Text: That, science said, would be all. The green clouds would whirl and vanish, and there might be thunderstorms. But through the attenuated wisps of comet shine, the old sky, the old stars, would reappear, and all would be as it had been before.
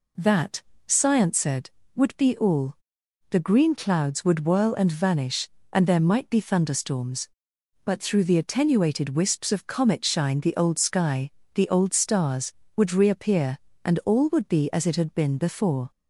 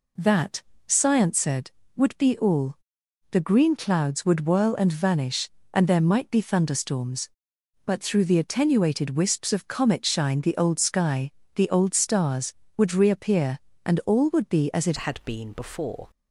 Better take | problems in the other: first | changes voice at "had"; from 14.9 s on; 1.1 s long

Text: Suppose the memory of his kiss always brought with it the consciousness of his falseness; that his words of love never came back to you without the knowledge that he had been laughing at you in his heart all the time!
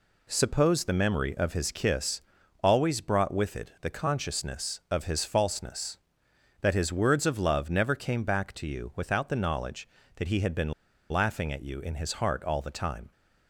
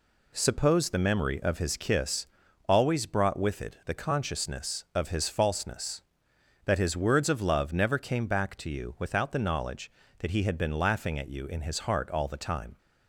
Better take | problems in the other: second | pauses between "kiss" and "always"; at 2.2 s; 0.42 s long; also in the second // pauses between "been" and "laughing"; at 10.7 s; 0.39 s long

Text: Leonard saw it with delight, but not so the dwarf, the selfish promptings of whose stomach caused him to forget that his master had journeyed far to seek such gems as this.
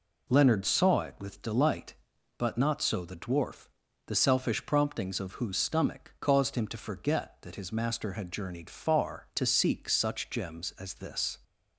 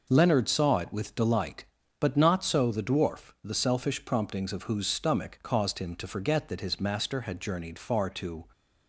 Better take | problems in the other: first | stops before "seek such gems as this"; at 8.5 s

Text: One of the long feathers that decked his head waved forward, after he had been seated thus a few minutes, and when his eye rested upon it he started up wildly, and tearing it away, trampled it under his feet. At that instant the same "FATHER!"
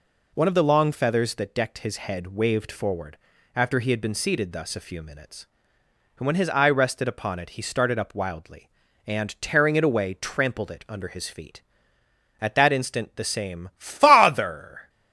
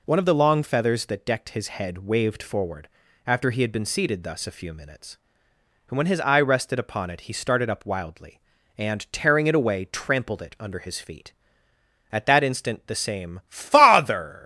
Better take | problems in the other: first | leaves "FATHER" unfinished; at 14.4 s; 145 ms

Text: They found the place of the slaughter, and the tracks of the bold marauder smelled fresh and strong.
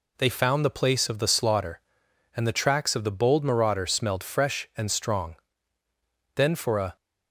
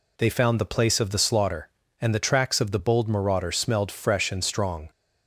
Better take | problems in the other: second | goes on to say "Then for a"; from 6.3 s on; 0.60 s long

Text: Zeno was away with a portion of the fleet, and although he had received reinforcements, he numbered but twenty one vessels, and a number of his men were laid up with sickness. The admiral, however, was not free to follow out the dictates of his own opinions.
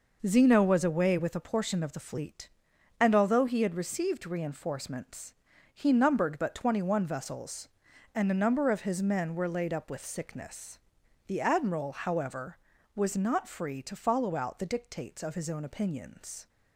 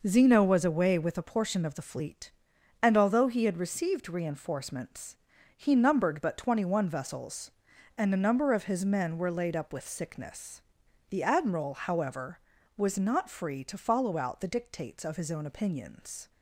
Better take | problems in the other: neither | none

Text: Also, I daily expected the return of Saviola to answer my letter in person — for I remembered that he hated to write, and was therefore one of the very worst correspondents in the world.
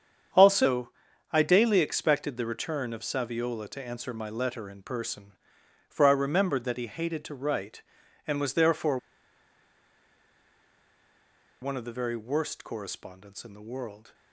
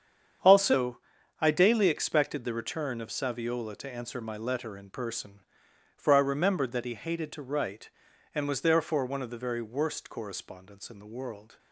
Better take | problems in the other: second | starts louder than the rest; strong; until 1.7 s; 7.5 dB; strong in the second // pauses between "therefore" and "one"; strong; at 8.9 s; 2.6 s long

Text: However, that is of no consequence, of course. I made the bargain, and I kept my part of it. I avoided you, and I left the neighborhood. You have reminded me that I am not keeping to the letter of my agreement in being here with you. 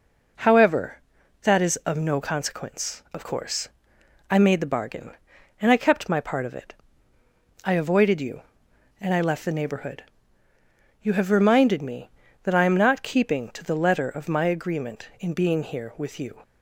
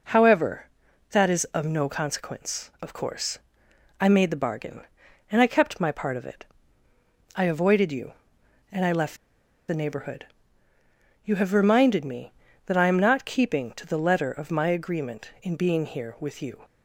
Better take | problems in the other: first | pauses between "left" and "the"; noticeable; at 9.1 s; 0.52 s long

